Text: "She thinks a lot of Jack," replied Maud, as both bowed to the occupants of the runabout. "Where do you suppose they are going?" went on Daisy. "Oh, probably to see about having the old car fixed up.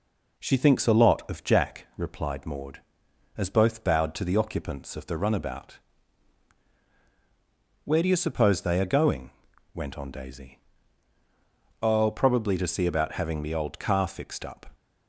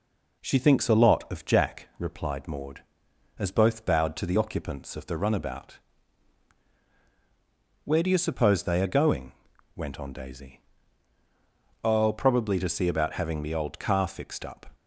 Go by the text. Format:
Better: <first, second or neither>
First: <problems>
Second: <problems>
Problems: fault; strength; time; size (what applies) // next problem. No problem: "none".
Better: neither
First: none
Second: none